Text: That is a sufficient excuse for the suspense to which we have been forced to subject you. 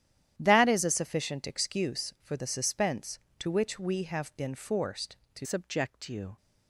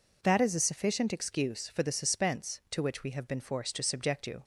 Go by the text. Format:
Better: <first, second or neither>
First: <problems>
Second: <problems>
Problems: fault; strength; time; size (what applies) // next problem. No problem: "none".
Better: second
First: starts louder than the rest; strong; until 1.3 s; 11 dB // changes voice at "subject"; from 5.4 s on; 0.9 s long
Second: none